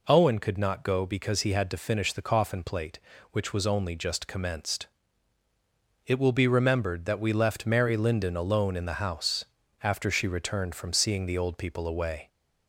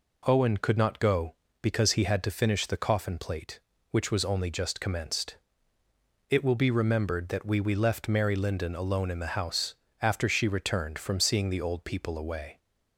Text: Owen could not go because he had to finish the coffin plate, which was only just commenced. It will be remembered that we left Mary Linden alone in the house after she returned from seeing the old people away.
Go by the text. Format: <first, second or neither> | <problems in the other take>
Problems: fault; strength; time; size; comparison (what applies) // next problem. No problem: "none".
first | says "we" twice; at 7.5 s // pauses between "house" and "after"; slight; at 9.7 s; 0.26 s long; slight in the first